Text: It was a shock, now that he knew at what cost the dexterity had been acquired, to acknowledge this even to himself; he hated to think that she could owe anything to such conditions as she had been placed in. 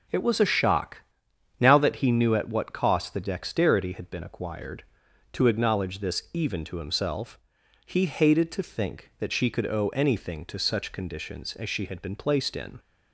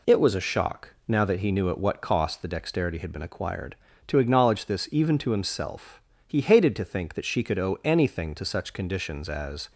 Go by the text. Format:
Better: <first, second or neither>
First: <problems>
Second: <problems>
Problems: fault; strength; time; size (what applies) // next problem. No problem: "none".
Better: first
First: none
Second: stops before "she had been placed in"; at 9.7 s